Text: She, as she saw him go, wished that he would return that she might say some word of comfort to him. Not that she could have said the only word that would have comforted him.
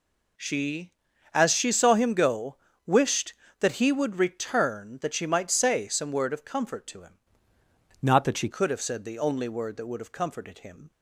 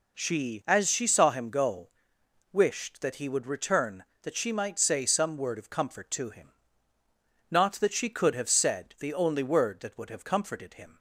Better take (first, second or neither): second